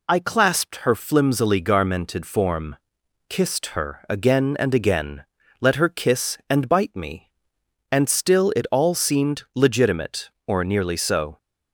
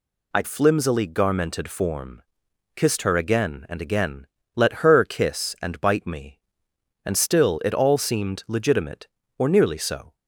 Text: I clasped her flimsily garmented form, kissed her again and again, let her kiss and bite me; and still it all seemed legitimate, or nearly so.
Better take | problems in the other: first | skips "clasped her"; at 0.4 s

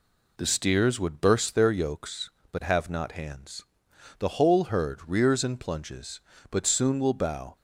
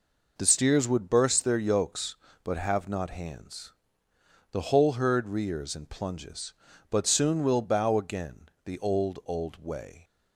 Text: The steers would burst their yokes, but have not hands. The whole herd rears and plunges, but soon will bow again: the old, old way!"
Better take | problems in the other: second | stops before "again the old old way"; at 7.5 s

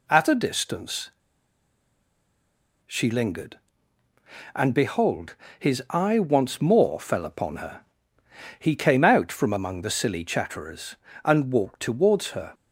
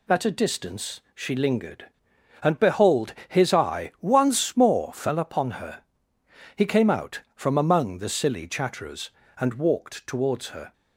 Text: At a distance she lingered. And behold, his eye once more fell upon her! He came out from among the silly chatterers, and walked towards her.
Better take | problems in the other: second | pauses between "distance" and "she"; strong; at 1.1 s; 1.7 s long

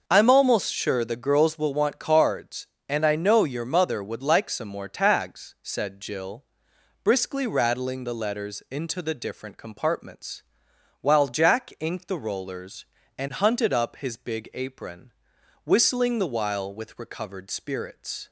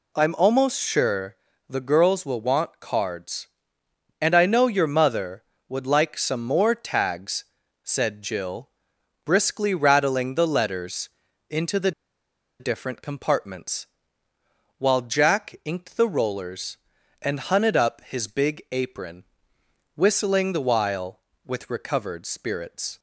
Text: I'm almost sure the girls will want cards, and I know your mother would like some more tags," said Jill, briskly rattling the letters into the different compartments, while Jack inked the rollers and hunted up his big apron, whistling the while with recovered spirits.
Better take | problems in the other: first | pauses between "sure" and "the"; slight; at 1.3 s; 0.34 s long // pauses between "letters" and "into"; at 11.0 s; 0.40 s long // pauses between "the" and "different"; noticeable; at 11.9 s; 0.69 s long

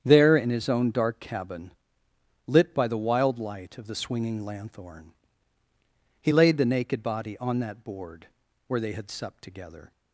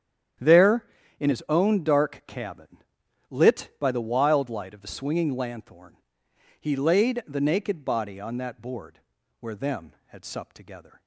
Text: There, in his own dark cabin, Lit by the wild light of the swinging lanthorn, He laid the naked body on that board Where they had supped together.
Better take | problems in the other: first | starts louder than the rest; strong; until 1.7 s; 9.5 dB; strong in the first // pauses between "board" and "Where"; at 8.9 s; 0.42 s long; also in the first // says "them" for "they"; at 9.5 s

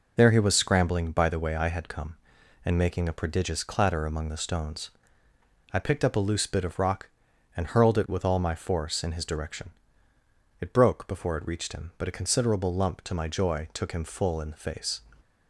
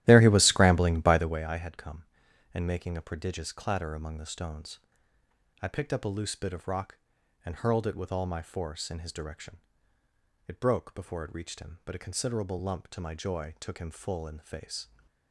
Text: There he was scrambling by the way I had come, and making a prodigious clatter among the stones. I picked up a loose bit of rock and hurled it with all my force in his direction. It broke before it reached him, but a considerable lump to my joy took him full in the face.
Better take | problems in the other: first | starts louder than the rest; strong; until 1.5 s; 13 dB

